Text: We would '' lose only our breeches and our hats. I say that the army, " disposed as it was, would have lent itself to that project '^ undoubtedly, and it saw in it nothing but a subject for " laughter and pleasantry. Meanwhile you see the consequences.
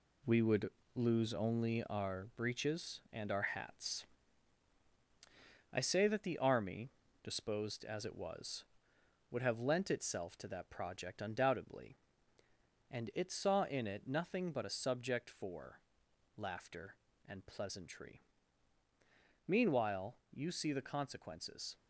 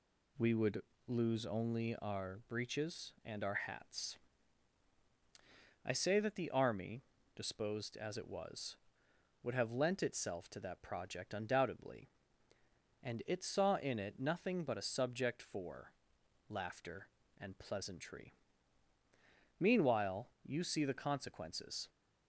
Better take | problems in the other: second | gets quieter; strong; throughout; 7.5 dB

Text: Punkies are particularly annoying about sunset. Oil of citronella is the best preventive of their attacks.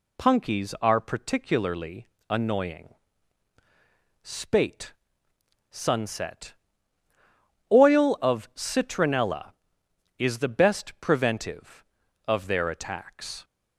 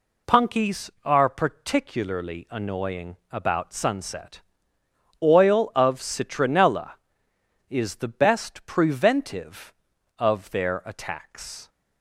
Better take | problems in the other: second | pauses between "particularly" and "annoying"; slight; at 2.0 s; 0.24 s long // says "spate" for "about"; at 4.2 s

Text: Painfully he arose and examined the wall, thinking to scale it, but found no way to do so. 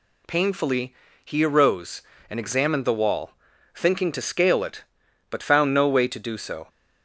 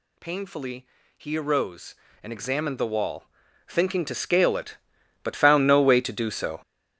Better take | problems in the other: first | gets louder; strong; throughout; 11 dB // pauses between "Painfully" and "he"; slight; at 0.8 s; 0.30 s long; slight in the first

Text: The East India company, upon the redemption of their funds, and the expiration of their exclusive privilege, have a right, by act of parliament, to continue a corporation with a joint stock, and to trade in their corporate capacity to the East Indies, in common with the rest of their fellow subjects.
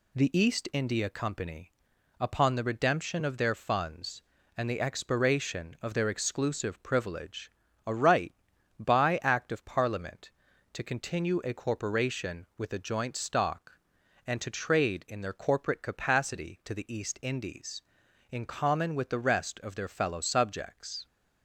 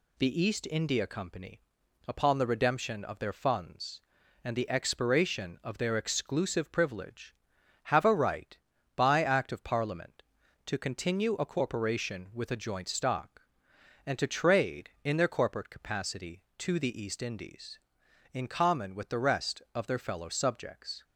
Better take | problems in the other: second | skips "have"; at 7.6 s

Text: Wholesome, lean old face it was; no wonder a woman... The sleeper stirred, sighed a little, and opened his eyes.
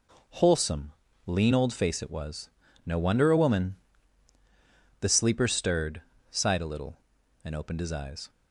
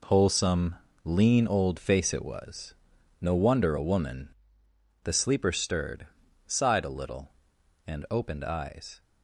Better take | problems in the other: first | skips "his"; at 8.4 s

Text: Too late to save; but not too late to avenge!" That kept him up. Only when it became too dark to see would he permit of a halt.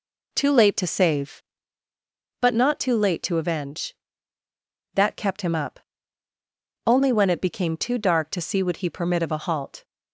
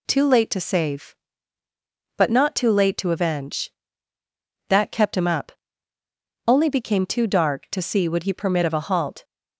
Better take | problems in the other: first | skips "when it"; at 6.6 s

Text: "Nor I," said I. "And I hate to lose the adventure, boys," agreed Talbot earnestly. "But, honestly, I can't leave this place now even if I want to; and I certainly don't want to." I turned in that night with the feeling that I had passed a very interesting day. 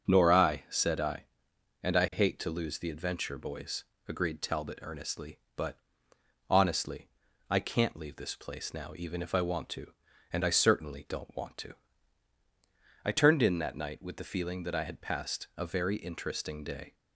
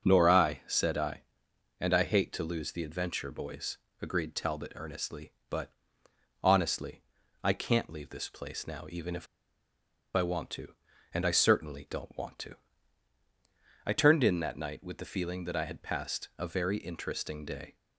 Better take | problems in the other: first | starts louder than the rest; until 1.0 s; 6 dB; also in the first // pauses between "if" and "I"; noticeable; at 9.2 s; 0.88 s long

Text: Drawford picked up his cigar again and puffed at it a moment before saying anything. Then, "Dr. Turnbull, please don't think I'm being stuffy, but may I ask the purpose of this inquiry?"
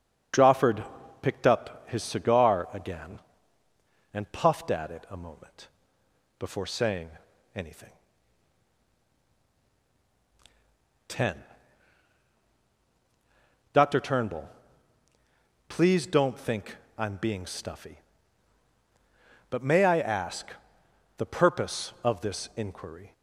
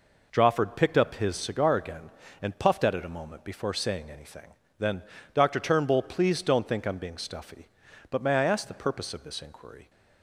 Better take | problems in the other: second | starts louder than the rest; strong; until 1.7 s; 7.5 dB // pauses between "Drawford" and "picked"; at 0.8 s; 0.38 s long // pauses between "moment" and "before"; noticeable; at 5.6 s; 0.72 s long // pauses between "saying" and "anything"; noticeable; at 7.0 s; 0.46 s long // says "Ten" for "Then"; at 11.0 s // pauses between "think" and "I'm"; slight; at 16.7 s; 0.20 s long // pauses between "ask" and "the"; noticeable; at 20.5 s; 0.66 s long

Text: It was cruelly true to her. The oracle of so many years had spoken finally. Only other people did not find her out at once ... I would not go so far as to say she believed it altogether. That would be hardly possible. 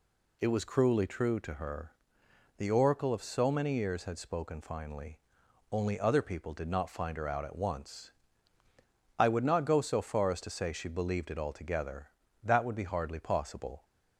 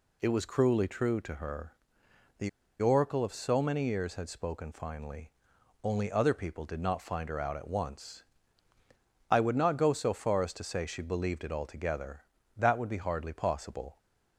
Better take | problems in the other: first | pauses between "The" and "oracle"; slight; at 2.4 s; 0.32 s long

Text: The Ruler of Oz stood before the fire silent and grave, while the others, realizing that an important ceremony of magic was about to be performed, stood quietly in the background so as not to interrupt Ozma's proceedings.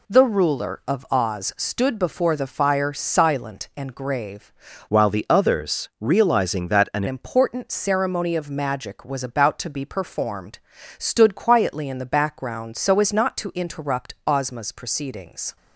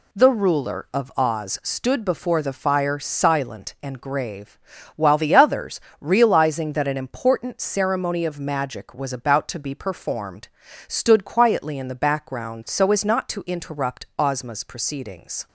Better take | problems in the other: second | changes voice from "while" to "an"; from 4.8 to 7.0 s; 2.2 s long

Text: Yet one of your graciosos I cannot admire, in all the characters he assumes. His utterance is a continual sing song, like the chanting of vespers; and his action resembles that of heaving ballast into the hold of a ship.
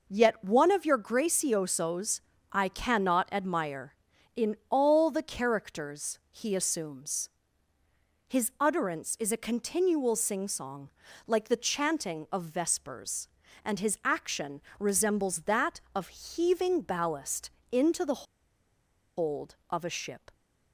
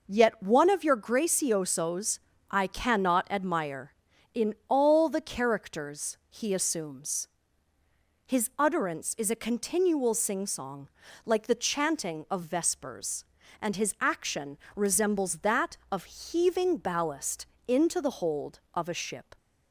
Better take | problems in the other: second | pauses between "graciosos" and "I"; slight; at 2.2 s; 0.32 s long; slight in the second // pauses between "action" and "resembles"; slight; at 14.6 s; 0.18 s long; slight in the second // pauses between "ballast" and "into"; slight; at 17.5 s; 0.22 s long; slight in the second // pauses between "the" and "hold"; noticeable; at 18.2 s; 0.94 s long

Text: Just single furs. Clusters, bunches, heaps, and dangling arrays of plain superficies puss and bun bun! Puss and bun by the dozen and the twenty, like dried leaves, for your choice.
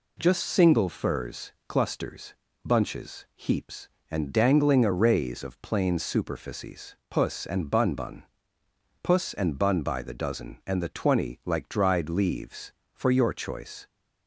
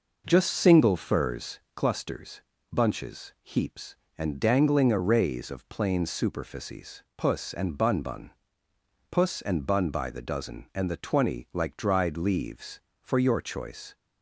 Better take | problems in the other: first | starts louder than the rest; noticeable; until 1.7 s; 5.5 dB

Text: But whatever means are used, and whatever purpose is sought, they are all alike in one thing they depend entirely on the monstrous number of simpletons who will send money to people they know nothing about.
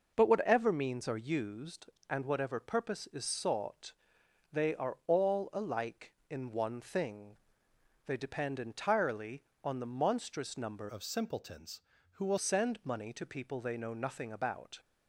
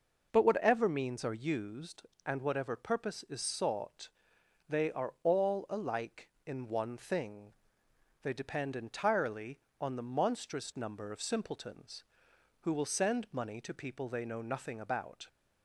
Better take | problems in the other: second | pauses between "thing" and "they"; noticeable; at 7.3 s; 0.70 s long; noticeable in the second // changes voice from "of" to "will"; from 10.8 to 12.3 s; 1.5 s long

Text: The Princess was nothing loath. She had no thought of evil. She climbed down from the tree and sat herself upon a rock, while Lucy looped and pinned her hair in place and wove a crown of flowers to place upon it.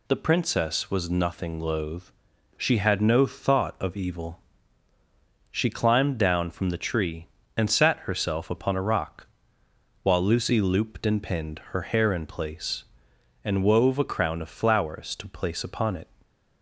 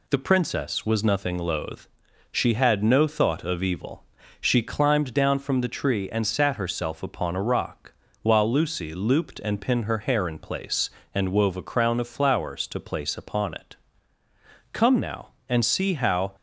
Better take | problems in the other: first | goes on to say "Come now and see how"; from 14.7 s on; 1.6 s long

